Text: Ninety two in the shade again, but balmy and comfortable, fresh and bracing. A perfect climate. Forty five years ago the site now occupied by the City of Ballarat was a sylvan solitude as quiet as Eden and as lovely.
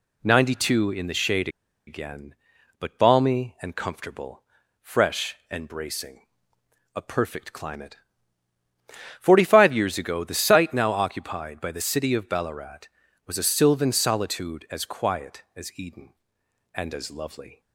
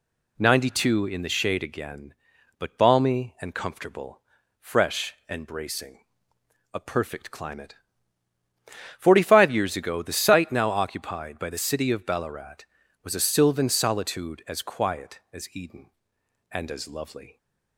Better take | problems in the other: second | pauses between "shade" and "again"; at 1.4 s; 0.38 s long

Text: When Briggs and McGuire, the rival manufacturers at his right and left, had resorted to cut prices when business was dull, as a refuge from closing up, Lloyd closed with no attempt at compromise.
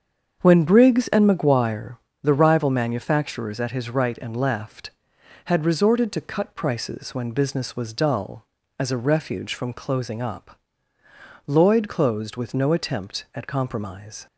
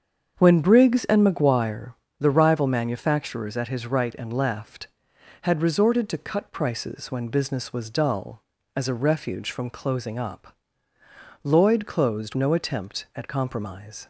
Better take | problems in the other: first | starts louder than the rest; strong; until 1.3 s; 7 dB; strong in the first // skips "with"; at 12.3 s

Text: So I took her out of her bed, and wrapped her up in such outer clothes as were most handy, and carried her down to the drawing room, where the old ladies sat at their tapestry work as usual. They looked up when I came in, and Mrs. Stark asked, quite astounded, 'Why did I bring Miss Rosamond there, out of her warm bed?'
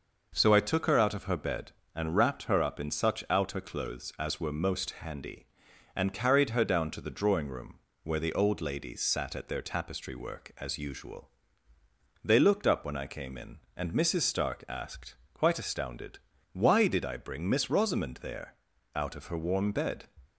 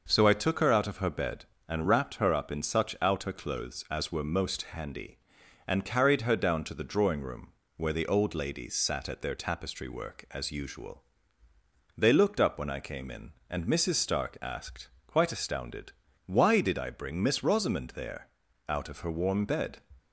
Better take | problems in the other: neither | none

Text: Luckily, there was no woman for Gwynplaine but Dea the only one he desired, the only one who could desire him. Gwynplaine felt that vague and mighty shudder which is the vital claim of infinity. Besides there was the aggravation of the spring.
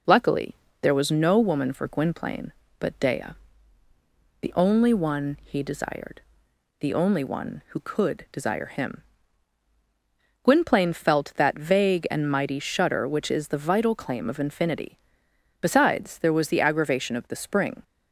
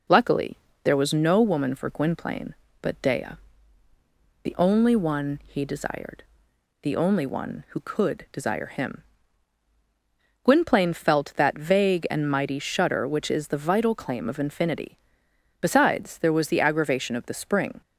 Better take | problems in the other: neither | pauses between "Dea" and "the"; the same in both

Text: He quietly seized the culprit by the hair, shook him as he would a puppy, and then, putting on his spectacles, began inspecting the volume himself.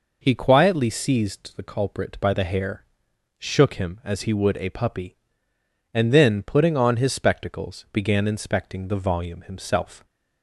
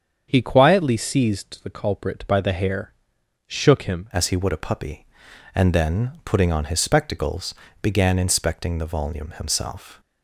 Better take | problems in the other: first | starts louder than the rest; strong; until 1.3 s; 7 dB // changes voice at "as"; from 4.1 s on; 5.8 s long

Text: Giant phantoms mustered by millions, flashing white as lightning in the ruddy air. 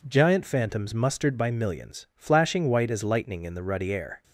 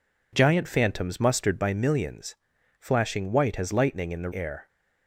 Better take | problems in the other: first | skips "ruddy"; at 4.3 s

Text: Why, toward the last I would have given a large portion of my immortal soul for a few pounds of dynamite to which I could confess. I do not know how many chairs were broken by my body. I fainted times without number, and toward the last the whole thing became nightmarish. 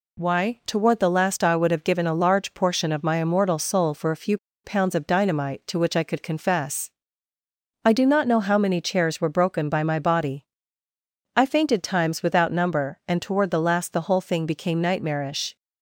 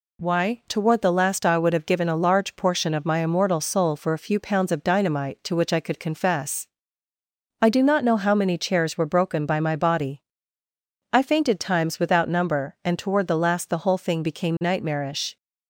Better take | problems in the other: second | pauses between "few" and "pounds"; slight; at 4.3 s; 0.28 s long

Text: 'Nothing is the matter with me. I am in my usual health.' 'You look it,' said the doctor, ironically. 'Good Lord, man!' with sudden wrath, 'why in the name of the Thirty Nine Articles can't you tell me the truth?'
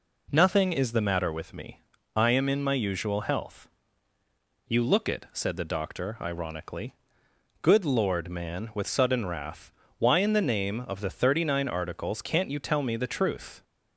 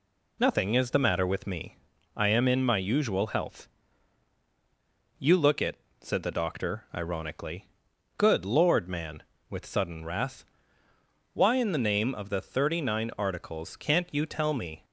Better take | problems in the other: first | stops before "the truth"; at 14.8 s

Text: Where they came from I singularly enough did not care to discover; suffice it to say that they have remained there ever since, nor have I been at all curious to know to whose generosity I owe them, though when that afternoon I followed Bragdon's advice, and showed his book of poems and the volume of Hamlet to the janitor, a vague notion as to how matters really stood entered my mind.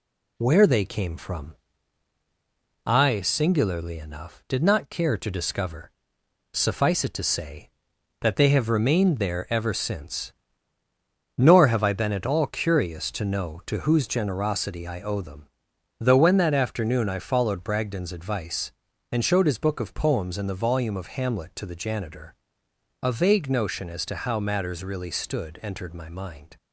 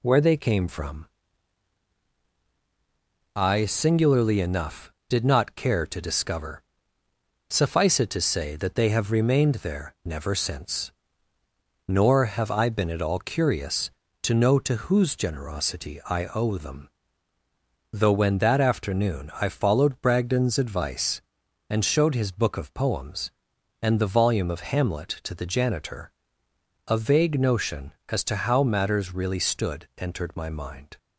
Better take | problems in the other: first | pauses between "from" and "I"; strong; at 1.0 s; 2.3 s long; strong in the first // says "never" for "ever"; at 10.0 s

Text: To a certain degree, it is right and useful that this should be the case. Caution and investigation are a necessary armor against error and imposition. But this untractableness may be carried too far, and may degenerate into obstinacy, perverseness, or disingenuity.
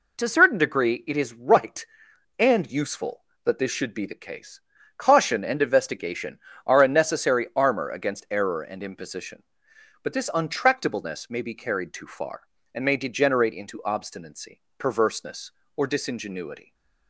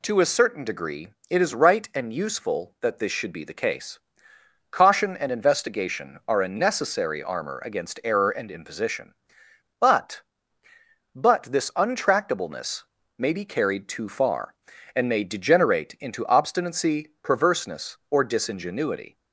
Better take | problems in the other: first | says "But" twice; at 11.1 s // pauses between "untractableness" and "may"; slight; at 12.8 s; 0.34 s long

